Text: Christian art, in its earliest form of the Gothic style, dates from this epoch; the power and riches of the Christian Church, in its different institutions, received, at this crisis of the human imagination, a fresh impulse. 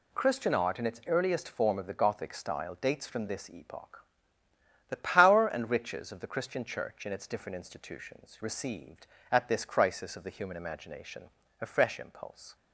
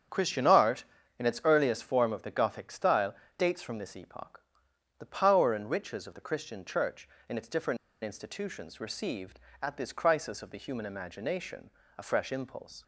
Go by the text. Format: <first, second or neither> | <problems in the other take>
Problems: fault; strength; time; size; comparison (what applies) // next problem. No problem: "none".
first | starts louder than the rest; strong; until 1.4 s; 8 dB // pauses between "different" and "institutions"; slight; at 7.7 s; 0.26 s long